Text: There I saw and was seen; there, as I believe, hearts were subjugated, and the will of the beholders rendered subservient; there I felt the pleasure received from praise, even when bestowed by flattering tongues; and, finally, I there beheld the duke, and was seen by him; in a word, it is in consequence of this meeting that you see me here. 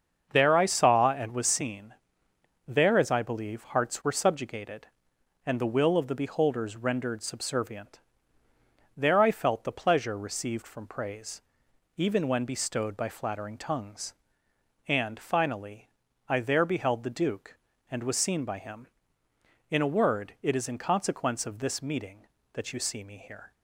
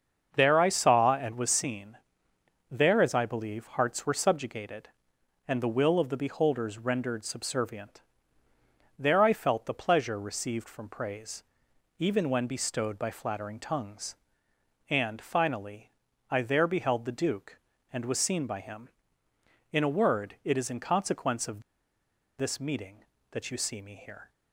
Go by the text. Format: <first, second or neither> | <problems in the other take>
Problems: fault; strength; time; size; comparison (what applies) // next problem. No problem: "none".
first | starts louder than the rest; until 1.3 s; 7 dB; also in the first // pauses between "of" and "this"; noticeable; at 21.6 s; 0.77 s long